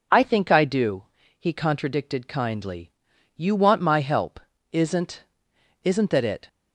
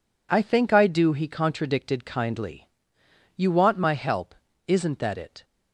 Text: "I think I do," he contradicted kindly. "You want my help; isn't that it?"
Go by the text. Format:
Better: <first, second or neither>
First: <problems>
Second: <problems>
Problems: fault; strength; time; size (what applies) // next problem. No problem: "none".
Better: second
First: says "isn't" twice; at 5.8 s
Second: none